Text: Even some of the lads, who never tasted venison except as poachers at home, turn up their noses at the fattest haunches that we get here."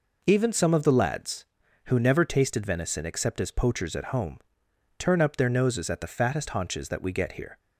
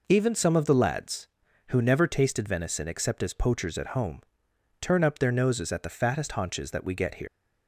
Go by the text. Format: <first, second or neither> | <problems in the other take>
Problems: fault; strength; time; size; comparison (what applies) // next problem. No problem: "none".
first | leaves "here" unfinished; at 7.2 s; 130 ms